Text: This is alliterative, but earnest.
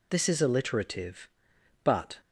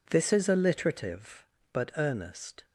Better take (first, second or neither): second